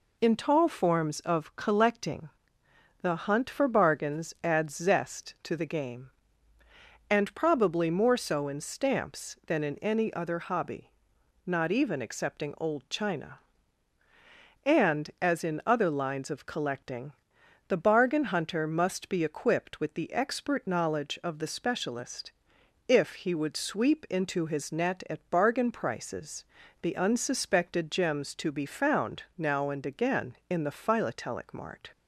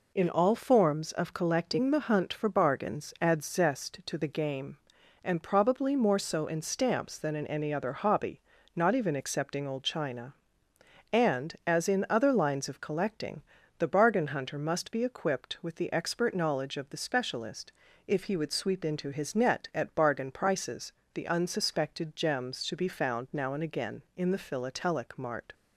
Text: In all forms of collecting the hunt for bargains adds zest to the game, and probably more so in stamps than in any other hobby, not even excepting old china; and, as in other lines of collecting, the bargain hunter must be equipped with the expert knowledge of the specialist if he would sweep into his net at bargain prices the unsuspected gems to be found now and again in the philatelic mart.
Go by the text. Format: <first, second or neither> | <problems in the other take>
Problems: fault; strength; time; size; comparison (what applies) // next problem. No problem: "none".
second | says "tall" for "all"; at 0.3 s // pauses between "collecting" and "the"; noticeable; at 2.2 s; 0.74 s long // pauses between "specialist" and "if"; noticeable; at 22.3 s; 0.56 s long; slight in the second // pauses between "prices" and "the"; at 26.4 s; 0.38 s long; slight in the second